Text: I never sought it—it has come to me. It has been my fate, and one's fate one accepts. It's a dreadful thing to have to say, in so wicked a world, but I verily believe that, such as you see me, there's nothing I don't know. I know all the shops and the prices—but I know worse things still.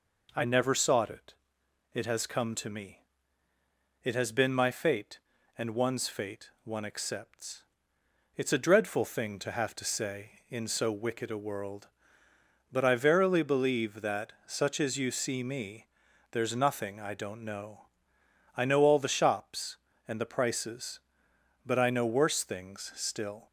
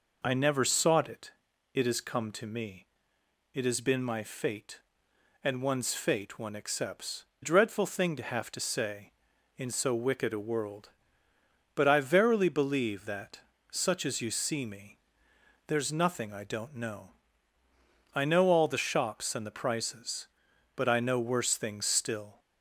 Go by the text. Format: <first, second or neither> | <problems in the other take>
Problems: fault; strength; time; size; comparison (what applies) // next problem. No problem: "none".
first | skips "It's a"; at 7.3 s